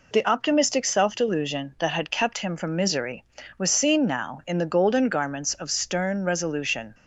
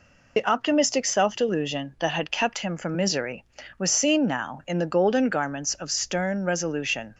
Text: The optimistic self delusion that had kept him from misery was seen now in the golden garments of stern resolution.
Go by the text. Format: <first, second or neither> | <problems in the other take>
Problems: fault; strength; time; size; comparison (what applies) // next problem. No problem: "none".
first | loses the start of "The"; at 0.3 s; 40 ms